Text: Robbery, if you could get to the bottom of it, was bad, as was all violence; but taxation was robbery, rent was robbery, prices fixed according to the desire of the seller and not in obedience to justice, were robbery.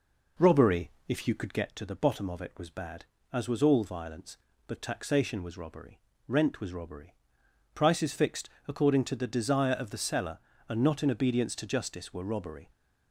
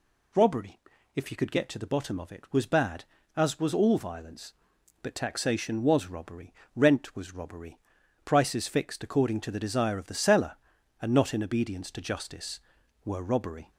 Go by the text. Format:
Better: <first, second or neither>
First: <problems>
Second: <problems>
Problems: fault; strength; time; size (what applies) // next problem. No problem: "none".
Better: second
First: starts louder than the rest; noticeable; until 1.7 s; 4.5 dB // pauses between "fixed" and "according"; slight; at 8.4 s; 0.20 s long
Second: none